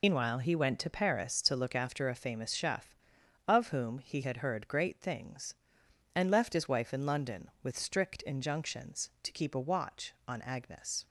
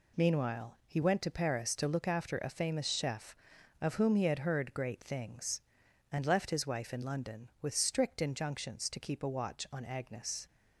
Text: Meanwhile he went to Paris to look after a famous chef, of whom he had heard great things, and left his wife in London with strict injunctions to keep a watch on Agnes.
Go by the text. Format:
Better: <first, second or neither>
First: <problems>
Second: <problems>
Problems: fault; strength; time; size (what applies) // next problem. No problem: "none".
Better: second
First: loses the start of "Meanwhile"; at 0.0 s; 110 ms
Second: none